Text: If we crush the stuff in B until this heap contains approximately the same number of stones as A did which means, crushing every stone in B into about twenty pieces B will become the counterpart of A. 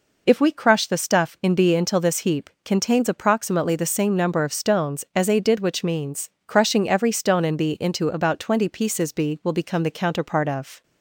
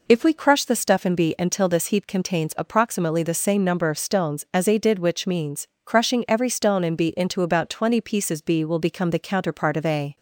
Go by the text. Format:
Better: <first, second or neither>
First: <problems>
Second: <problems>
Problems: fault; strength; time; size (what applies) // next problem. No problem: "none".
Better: second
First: stops before "A"; at 10.8 s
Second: none